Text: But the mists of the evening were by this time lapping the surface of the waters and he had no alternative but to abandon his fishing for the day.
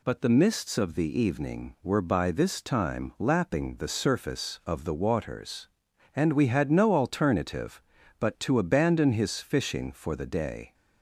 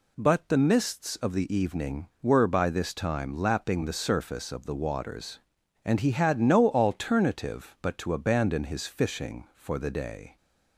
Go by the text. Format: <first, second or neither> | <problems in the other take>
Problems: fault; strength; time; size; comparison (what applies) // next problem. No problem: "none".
second | says "we" for "he"; at 6.3 s